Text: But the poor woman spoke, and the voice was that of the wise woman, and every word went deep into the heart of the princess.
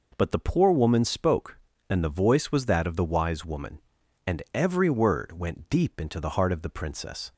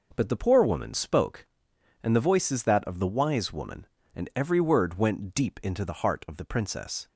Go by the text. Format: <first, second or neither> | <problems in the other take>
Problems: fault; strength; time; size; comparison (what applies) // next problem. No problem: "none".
first | says "is" for "was"; at 2.5 s